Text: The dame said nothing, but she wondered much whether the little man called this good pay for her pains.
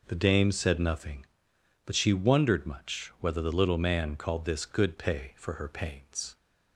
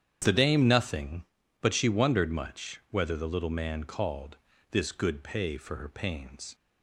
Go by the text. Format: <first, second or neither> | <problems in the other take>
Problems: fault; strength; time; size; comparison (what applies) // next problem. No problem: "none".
first | starts louder than the rest; strong; until 1.2 s; 9 dB // skips "said"; at 0.6 s // pauses between "called" and "this"; slight; at 4.3 s; 0.34 s long